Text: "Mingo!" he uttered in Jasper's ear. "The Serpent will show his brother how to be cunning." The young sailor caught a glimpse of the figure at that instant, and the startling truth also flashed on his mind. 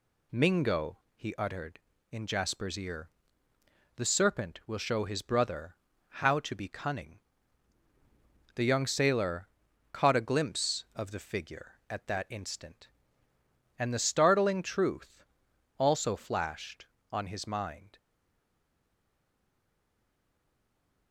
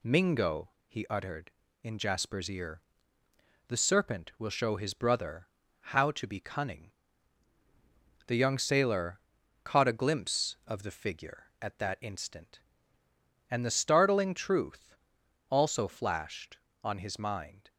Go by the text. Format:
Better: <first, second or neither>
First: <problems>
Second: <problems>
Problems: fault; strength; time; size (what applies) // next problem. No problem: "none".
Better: second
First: pauses between "brother" and "how"; slight; at 5.7 s; 0.32 s long // pauses between "sailor" and "caught"; noticeable; at 9.4 s; 0.46 s long // pauses between "truth" and "also"; noticeable; at 15.2 s; 0.54 s long // stays silent after the last word; strong; from 17.9 s on; 3.2 s long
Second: pauses between "brother" and "how"; slight; at 5.4 s; 0.32 s long // pauses between "sailor" and "caught"; noticeable; at 9.1 s; 0.46 s long // pauses between "truth" and "also"; noticeable; at 14.9 s; 0.54 s long